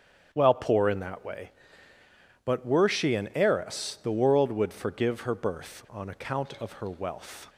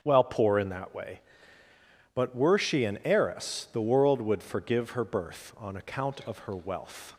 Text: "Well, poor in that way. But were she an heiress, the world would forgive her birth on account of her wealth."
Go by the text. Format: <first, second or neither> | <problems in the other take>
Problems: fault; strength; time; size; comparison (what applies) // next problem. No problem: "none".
neither | starts louder than the rest; strong; the same in both